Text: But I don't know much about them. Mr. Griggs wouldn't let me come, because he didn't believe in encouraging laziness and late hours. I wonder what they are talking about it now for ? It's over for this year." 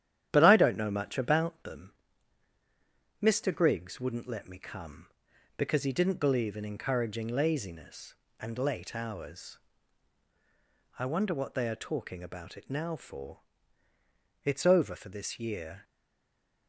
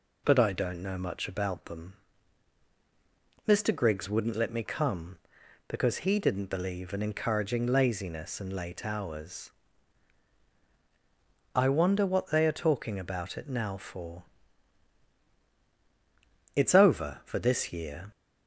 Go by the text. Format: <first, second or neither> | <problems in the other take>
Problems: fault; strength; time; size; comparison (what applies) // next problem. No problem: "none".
second | starts louder than the rest; strong; until 1.3 s; 10.5 dB // stays silent after the last word; slight; from 15.8 s on; 0.8 s long